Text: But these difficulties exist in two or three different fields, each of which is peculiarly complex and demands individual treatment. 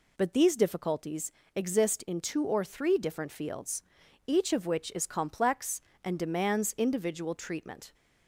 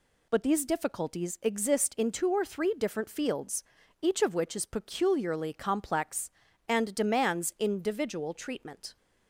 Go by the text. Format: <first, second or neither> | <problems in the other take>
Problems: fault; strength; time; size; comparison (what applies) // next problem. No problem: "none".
second | pauses between "difficulties" and "exist"; slight; at 1.3 s; 0.24 s long // skips "peculiarly"; at 5.0 s